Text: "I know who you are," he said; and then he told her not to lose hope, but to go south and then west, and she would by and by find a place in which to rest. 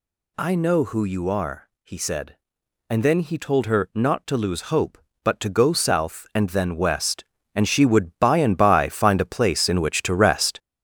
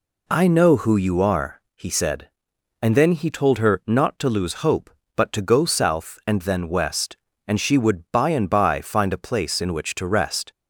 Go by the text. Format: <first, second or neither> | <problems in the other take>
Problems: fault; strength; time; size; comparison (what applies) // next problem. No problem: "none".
second | gets louder; throughout; 6 dB